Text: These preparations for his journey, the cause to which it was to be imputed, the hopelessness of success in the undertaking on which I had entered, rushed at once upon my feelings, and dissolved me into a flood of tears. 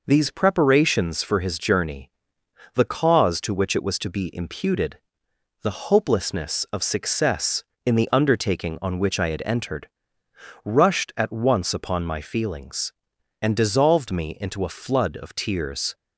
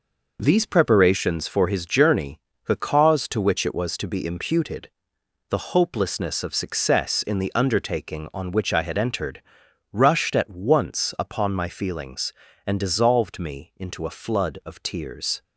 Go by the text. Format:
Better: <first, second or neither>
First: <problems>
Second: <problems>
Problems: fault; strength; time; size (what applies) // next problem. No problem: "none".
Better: neither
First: none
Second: none